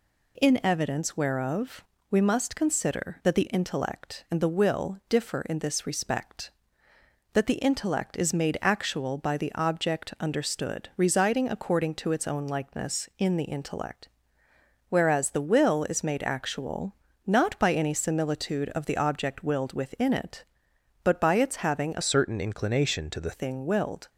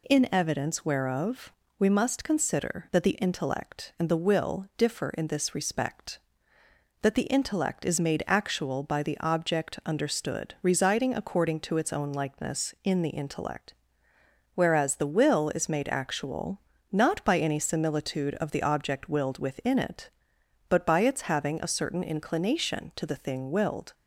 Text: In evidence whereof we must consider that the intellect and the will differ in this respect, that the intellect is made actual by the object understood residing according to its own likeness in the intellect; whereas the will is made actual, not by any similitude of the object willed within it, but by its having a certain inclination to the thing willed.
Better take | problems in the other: second | pauses between "whereof" and "we"; slight; at 1.8 s; 0.28 s long; slight in the second // changes voice from "certain" to "the"; from 22.0 to 23.3 s; 1.3 s long

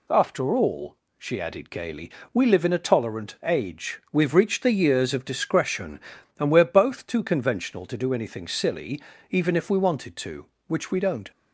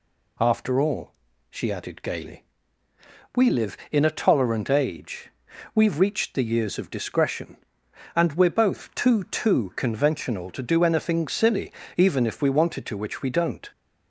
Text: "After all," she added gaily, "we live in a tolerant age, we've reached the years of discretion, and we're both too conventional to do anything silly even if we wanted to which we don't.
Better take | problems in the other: first | says "too" twice; at 9.2 s // pauses between "silly" and "even"; slight; at 11.7 s; 0.24 s long; slight in the first

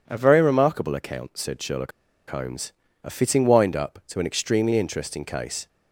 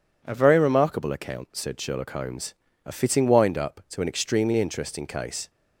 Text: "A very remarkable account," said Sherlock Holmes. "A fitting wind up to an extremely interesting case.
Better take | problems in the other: second | pauses between "Sherlock" and "Holmes"; at 1.9 s; 0.39 s long

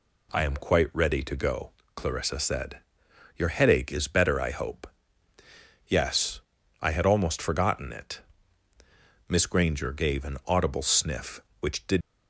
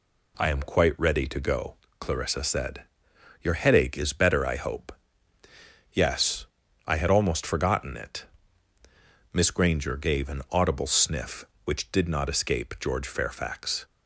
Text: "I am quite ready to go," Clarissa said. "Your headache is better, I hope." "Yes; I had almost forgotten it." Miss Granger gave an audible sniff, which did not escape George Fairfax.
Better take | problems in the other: second | stops before "not escape George Fairfax"; at 12.0 s

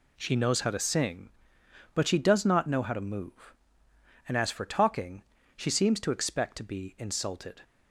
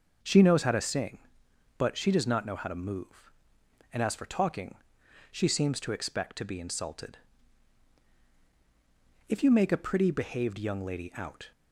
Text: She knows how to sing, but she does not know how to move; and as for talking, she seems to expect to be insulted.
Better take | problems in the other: first | starts louder than the rest; noticeable; until 1.8 s; 6 dB // goes on to say "If you make a pretty behaved young lady out"; strong; from 9.2 s on; 2.2 s long

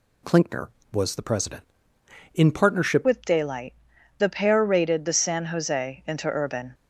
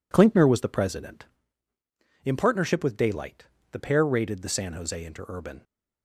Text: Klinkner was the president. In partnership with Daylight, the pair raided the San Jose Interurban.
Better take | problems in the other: second | changes voice at "with"; from 3.0 s on; 3.7 s long

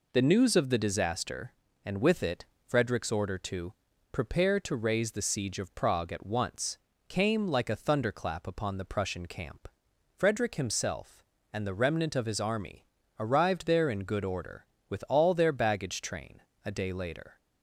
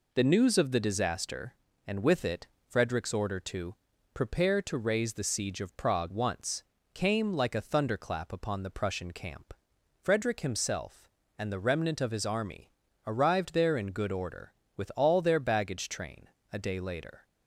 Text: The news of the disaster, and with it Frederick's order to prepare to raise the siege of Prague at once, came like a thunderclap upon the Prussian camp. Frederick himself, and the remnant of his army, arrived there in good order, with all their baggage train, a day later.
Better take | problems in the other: first | pauses between "it" and "Frederick's"; slight; at 2.4 s; 0.20 s long; slight in the first // pauses between "to" and "prepare"; at 3.7 s; 0.38 s long; also in the first // skips "at"; at 6.1 s

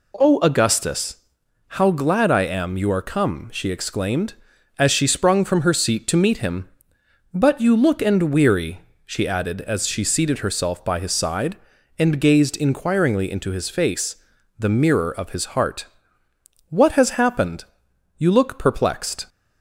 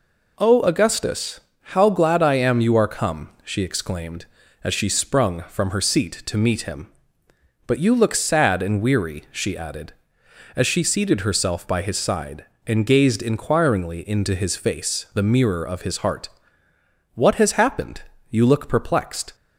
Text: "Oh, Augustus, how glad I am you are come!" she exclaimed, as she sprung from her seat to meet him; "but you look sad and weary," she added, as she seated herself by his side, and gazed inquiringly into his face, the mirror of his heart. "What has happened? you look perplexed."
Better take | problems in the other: second | skips "sad"; at 8.0 s

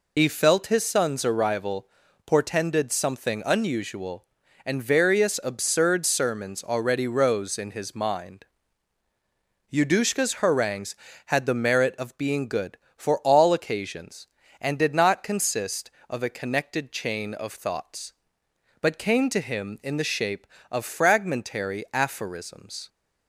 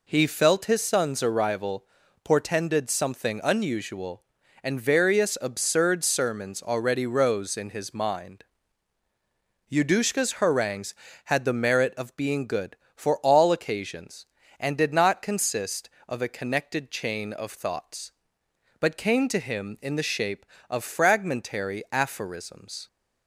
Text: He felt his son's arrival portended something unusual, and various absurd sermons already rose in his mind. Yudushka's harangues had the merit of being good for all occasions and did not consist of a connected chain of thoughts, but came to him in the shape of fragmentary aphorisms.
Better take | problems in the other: second | loses the start of "He"; at 0.1 s; 75 ms // pauses between "arrival" and "portended"; at 1.8 s; 0.40 s long; also in the second

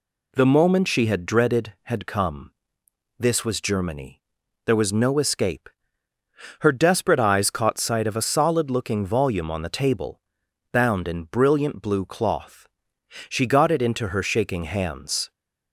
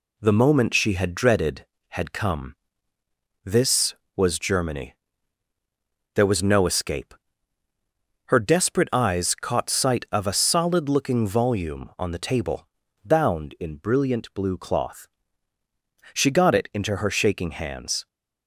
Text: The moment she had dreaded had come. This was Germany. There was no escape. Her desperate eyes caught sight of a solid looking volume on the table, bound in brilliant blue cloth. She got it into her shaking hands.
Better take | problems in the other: neither | none

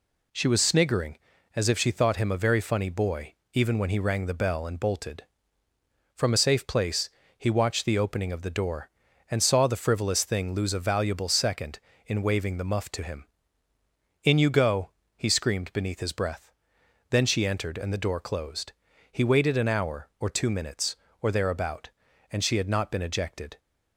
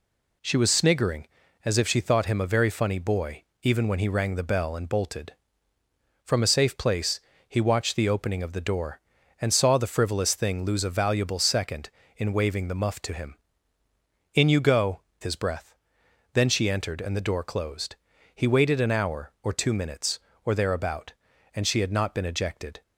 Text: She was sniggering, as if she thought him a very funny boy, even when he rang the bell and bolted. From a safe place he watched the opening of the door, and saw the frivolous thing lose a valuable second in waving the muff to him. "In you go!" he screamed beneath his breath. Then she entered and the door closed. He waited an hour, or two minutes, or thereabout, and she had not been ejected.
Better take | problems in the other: first | pauses between "place" and "he"; slight; at 7.1 s; 0.28 s long; slight in the first // skips "he screamed beneath"; at 15.1 s

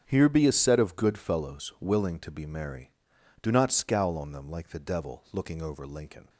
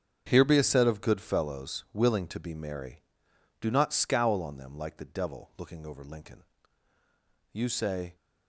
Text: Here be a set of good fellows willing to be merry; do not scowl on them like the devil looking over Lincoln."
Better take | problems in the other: first | starts louder than the rest; strong; until 1.3 s; 7.5 dB; strong in the first // goes on to say "You say"; noticeable; from 7.5 s on; 0.62 s long

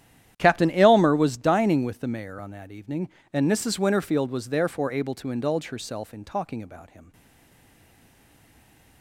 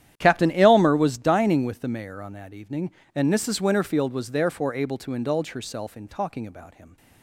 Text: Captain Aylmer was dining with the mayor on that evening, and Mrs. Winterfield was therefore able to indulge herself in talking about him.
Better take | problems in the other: second | starts louder than the rest; strong; until 1.3 s; 10.5 dB; strong in the second // stays silent after the last word; noticeable; from 7.1 s on; 1.9 s long

